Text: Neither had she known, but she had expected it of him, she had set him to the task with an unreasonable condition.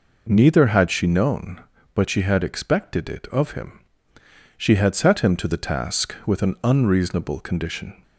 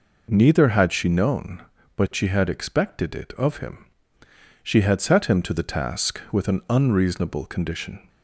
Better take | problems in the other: neither | none

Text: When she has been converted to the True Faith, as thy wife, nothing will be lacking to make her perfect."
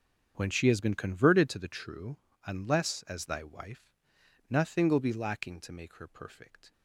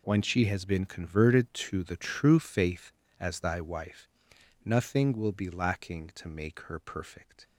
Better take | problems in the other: second | starts louder than the rest; until 1.3 s; 7 dB // says "Unless" for "Faith"; at 2.4 s

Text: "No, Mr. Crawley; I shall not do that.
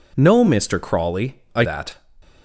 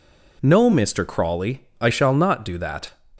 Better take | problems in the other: second | skips "shall not do"; at 1.6 s

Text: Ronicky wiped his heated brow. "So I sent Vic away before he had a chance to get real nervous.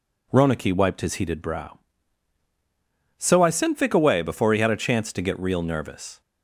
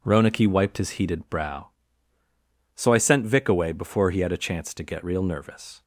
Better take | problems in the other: neither | none

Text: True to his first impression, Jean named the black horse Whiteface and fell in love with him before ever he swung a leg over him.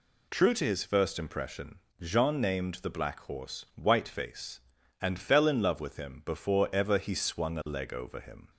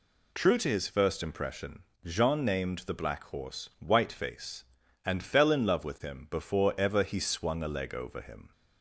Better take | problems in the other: neither | none

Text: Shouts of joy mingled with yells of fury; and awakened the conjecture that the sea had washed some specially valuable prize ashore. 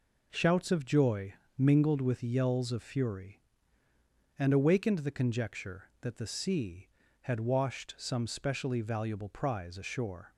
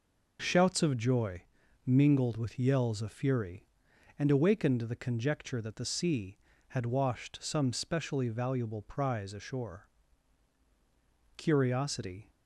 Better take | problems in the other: first | pauses between "joy" and "mingled"; at 1.4 s; 0.42 s long; slight in the first // goes on to say "Curiosity"; noticeable; from 11.3 s on; 0.94 s long

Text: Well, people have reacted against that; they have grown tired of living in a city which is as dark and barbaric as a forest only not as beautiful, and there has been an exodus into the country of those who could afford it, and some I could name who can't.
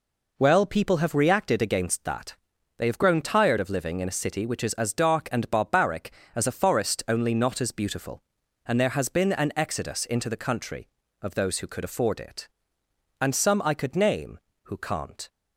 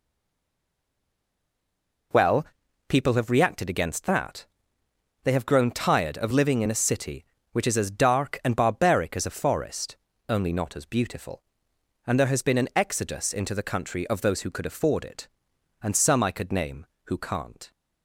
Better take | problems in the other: first | stays silent before the first word; until 2.1 s; 2.1 s long // pauses between "forest" and "only"; slight; at 9.9 s; 0.32 s long

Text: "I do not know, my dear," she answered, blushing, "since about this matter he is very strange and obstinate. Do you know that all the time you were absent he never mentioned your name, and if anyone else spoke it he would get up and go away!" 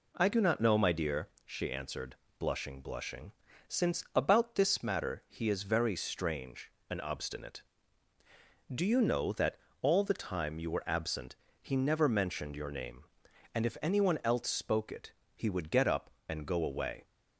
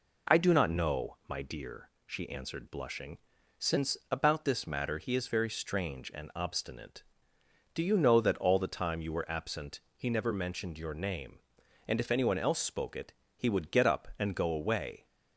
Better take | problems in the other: second | says "blushing" twice; at 2.8 s // pauses between "that" and "all"; slight; at 9.5 s; 0.22 s long // pauses between "absent" and "he"; slight; at 11.3 s; 0.26 s long; slight in the second // pauses between "it" and "he"; slight; at 15.1 s; 0.24 s long; slight in the second

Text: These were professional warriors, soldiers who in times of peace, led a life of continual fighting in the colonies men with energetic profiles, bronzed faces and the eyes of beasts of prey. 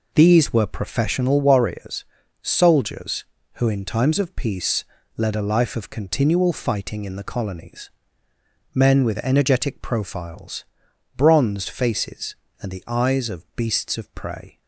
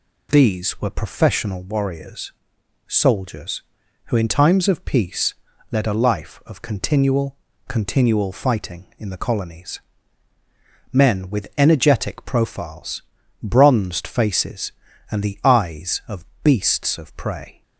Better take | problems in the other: first | says "continual" twice; at 7.6 s // pauses between "colonies" and "men"; at 9.8 s; 1.1 s long; noticeable in the first // pauses between "of" and "beasts"; slight; at 16.2 s; 0.18 s long

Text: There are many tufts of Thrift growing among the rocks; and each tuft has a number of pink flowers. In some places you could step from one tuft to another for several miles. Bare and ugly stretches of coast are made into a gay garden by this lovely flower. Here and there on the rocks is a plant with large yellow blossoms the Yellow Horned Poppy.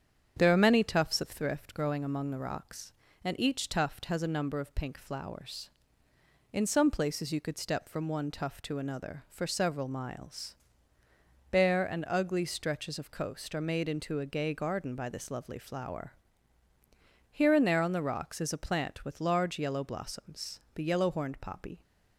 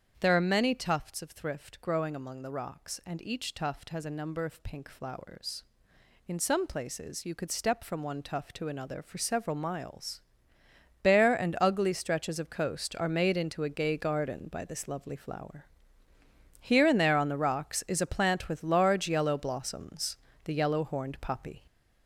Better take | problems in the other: first | gets louder; noticeable; throughout; 5.5 dB // starts louder than the rest; strong; until 1.2 s; 8 dB; strong in the first // pauses between "blossoms" and "the"; slight; at 20.1 s; 0.30 s long; slight in the first

